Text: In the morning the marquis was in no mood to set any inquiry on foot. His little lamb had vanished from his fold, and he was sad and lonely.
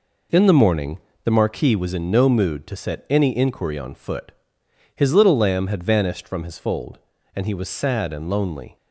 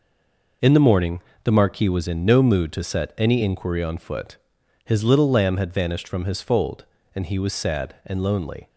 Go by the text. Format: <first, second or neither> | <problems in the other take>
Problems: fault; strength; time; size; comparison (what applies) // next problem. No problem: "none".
first | stays silent before the first word; slight; until 0.6 s; 0.6 s long // pauses between "morning" and "the"; slight; at 1.1 s; 0.24 s long; slight in the first